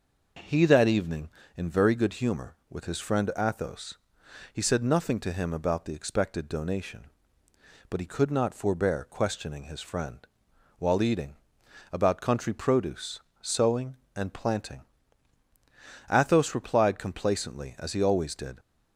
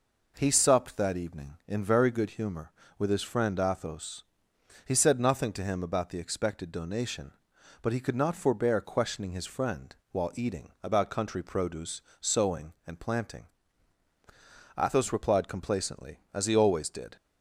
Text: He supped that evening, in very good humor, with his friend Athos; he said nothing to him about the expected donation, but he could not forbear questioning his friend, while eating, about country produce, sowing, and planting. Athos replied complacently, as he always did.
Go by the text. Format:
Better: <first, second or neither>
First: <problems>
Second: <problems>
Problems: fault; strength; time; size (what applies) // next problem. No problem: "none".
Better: second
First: skips "supped"; at 0.6 s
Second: none